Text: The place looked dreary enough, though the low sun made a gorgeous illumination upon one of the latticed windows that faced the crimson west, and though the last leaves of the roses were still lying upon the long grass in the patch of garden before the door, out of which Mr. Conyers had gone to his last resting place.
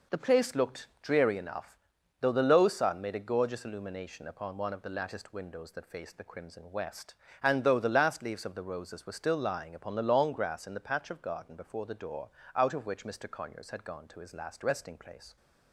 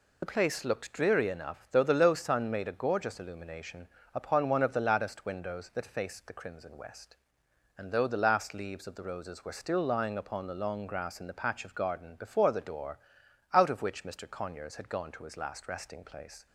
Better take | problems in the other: first | loses the start of "The"; at 0.2 s; 55 ms // pauses between "illumination" and "upon"; slight; at 3.8 s; 0.24 s long

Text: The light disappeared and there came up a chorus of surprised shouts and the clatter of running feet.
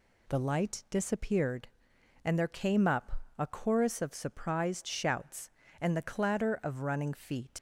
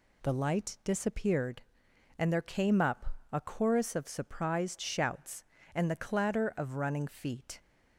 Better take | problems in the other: second | pauses between "up" and "a"; slight; at 3.2 s; 0.16 s long; slight in the second // leaves "feet" unfinished; at 7.5 s; 75 ms

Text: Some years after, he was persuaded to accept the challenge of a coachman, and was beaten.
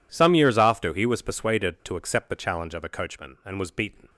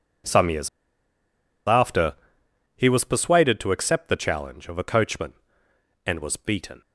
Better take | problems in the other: first | pauses between "years" and "after"; at 0.6 s; 1.0 s long

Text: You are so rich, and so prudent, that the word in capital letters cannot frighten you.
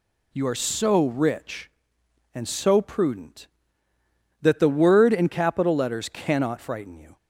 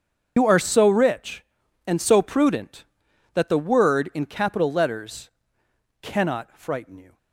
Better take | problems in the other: first | loses the start of "You"; at 0.3 s; 85 ms // starts louder than the rest; until 1.3 s; 7 dB // pauses between "letters" and "cannot"; noticeable; at 5.2 s; 0.72 s long

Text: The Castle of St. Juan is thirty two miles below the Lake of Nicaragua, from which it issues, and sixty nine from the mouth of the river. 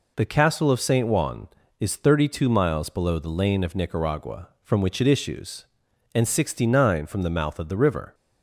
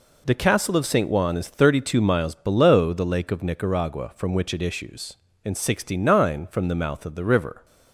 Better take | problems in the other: second | says "Lane" for "Lake"; at 3.2 s

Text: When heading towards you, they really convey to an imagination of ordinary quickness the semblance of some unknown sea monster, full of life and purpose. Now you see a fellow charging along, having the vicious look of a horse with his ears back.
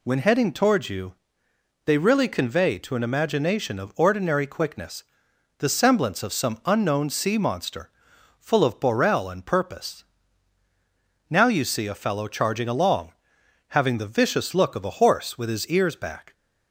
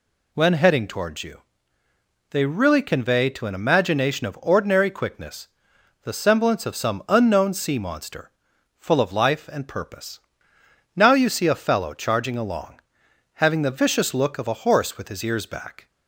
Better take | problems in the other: second | pauses between "quickness" and "the"; noticeable; at 5.0 s; 0.56 s long; noticeable in the second // says "borel" for "life"; at 8.8 s

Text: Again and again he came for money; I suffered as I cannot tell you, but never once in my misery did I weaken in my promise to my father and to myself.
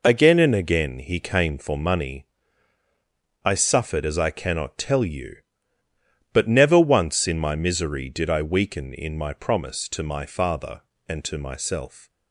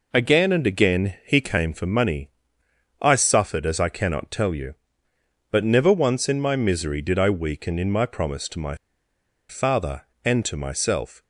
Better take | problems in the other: first | pauses between "my" and "father"; noticeable; at 8.7 s; 0.74 s long

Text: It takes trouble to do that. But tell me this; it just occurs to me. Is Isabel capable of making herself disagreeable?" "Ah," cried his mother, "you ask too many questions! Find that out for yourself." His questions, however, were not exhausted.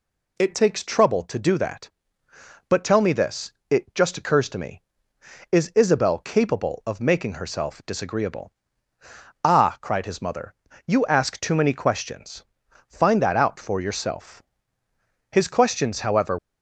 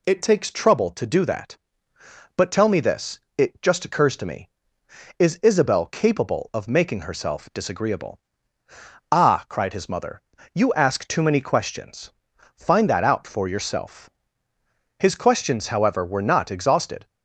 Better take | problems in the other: second | stops before "were not exhausted"; at 16.3 s

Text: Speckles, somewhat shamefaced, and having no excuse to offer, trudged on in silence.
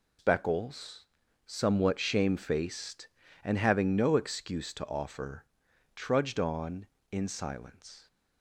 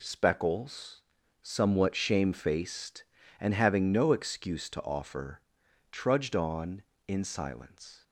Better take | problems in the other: second | loses the start of "Speckles"; at 0.1 s; 150 ms

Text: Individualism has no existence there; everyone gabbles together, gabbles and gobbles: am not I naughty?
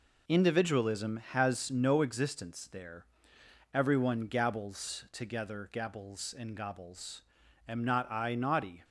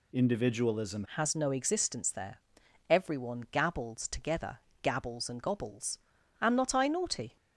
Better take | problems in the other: first | changes voice at "has"; from 1.1 s on; 6.2 s long

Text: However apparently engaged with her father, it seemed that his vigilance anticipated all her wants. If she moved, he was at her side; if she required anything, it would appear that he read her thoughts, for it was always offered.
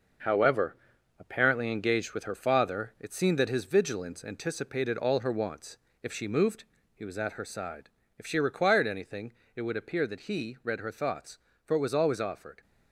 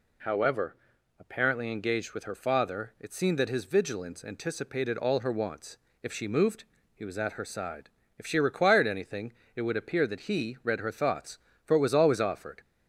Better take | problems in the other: second | gets quieter; throughout; 6.5 dB // pauses between "However" and "apparently"; at 0.7 s; 0.44 s long; also in the second

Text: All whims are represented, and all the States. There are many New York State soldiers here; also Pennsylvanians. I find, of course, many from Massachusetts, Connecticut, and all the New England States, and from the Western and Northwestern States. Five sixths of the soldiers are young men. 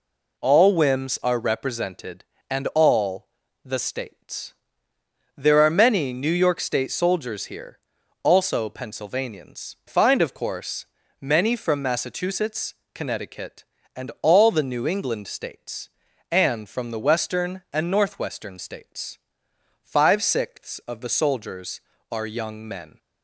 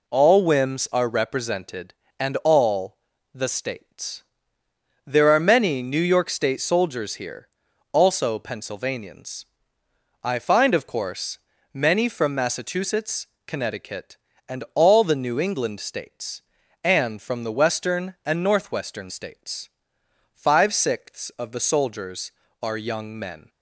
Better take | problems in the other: second | pauses between "all" and "the"; at 3.2 s; 0.38 s long; also in the second // skips "I"; at 9.8 s

